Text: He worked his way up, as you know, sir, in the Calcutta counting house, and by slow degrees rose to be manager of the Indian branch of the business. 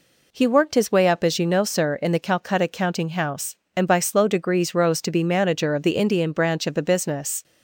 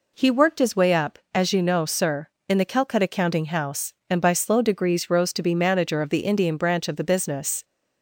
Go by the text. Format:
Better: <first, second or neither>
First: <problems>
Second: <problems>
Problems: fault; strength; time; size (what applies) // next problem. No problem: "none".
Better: neither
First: none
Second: none